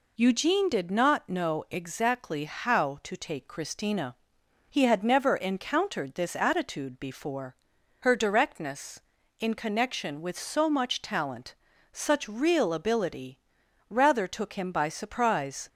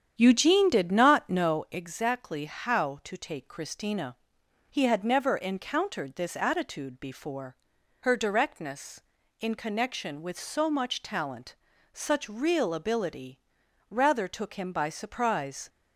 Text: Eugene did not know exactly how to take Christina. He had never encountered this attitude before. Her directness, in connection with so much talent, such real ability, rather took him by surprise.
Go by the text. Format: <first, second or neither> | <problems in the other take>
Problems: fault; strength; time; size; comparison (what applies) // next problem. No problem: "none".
first | starts louder than the rest; strong; until 1.7 s; 9 dB